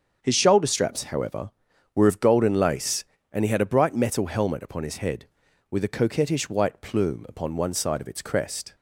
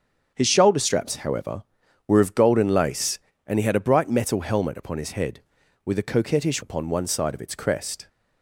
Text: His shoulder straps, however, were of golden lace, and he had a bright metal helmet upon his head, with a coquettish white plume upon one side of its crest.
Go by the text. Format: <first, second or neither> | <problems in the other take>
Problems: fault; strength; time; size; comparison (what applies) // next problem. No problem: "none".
first | starts louder than the rest; strong; until 1.3 s; 7 dB; also in the first // skips "white plume"; at 6.6 s